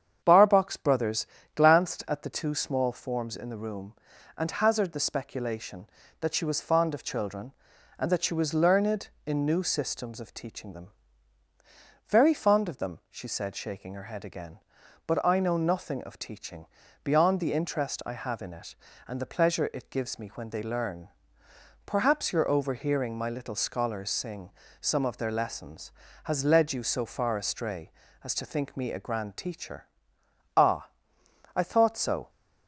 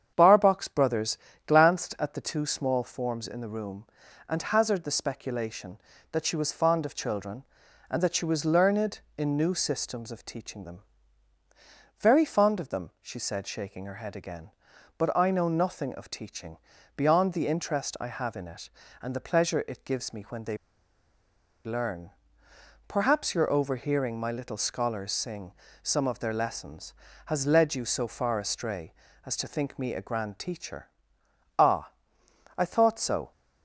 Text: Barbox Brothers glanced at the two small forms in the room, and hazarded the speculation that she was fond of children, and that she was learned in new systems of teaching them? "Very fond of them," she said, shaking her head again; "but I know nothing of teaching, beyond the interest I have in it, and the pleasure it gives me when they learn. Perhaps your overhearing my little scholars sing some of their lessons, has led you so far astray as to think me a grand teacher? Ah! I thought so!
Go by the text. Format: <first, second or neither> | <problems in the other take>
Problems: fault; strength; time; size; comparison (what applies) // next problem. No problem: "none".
first | starts louder than the rest; strong; until 1.1 s; 8 dB; strong in the first // pauses between "Brothers" and "glanced"; slight; at 1.1 s; 0.30 s long; slight in the first // pauses between "they" and "learn"; at 20.5 s; 1.0 s long // pauses between "sing" and "some"; slight; at 25.5 s; 0.30 s long; slight in the first